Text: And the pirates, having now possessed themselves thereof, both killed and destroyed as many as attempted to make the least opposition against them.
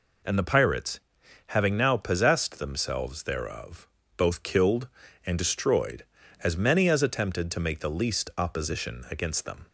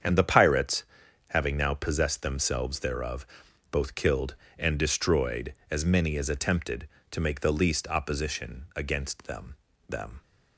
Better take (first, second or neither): first